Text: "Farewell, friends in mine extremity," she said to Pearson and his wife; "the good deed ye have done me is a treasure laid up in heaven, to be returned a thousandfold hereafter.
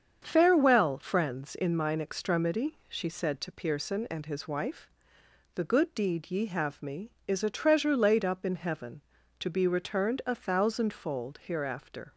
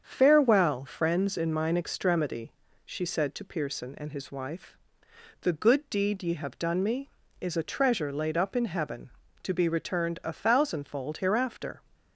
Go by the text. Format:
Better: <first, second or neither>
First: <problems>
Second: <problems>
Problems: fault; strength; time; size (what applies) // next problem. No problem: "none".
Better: second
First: starts louder than the rest; strong; until 1.2 s; 7.5 dB // skips "done"; at 6.8 s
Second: starts louder than the rest; strong; until 1.0 s; 7.5 dB